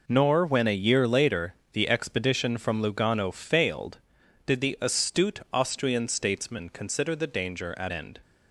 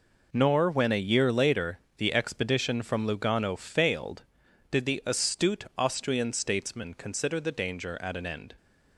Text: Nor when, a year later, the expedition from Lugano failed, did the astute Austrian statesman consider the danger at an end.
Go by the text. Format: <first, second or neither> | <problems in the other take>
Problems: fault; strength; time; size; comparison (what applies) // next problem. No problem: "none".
second | skips "an"; at 7.9 s